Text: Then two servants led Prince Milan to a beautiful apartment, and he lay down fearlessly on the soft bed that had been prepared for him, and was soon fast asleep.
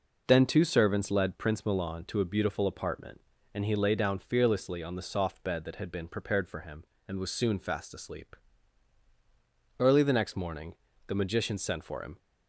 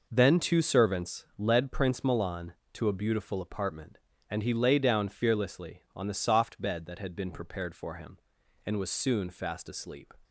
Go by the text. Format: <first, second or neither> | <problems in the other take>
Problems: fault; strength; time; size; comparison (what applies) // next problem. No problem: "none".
second | goes on to say "Early the next morning the Magician sent for him"; strong; from 9.7 s on; 2.4 s long